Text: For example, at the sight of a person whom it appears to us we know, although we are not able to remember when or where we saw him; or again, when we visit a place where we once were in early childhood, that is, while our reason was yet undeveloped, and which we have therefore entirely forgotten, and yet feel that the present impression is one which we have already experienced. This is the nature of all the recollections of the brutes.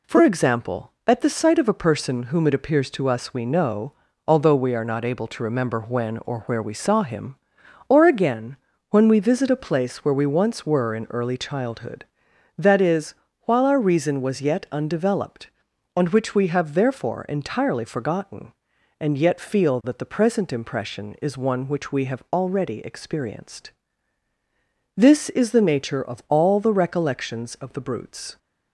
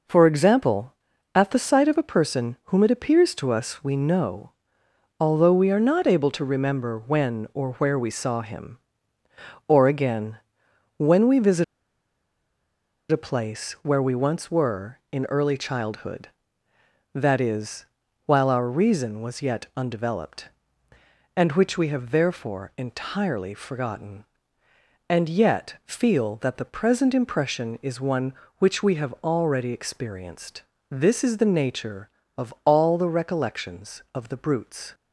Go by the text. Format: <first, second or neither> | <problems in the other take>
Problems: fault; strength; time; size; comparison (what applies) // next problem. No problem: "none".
first | pauses between "visit" and "a"; strong; at 11.6 s; 1.4 s long